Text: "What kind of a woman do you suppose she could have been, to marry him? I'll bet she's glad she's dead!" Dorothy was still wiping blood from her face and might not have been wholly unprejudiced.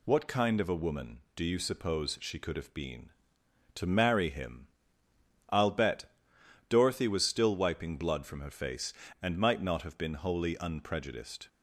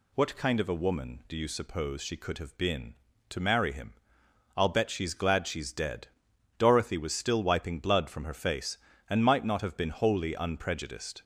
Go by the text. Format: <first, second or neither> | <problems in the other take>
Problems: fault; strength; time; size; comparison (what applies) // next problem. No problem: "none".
second | skips "she's glad she's dead"; at 6.3 s